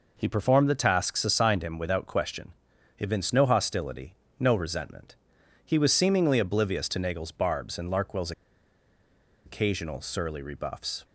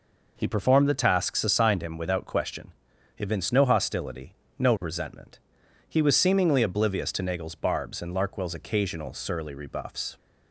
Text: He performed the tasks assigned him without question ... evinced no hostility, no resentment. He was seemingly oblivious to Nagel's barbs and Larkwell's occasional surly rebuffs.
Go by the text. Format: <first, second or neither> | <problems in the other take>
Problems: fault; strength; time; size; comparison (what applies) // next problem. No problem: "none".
second | pauses between "Larkwell's" and "occasional"; at 8.3 s; 1.1 s long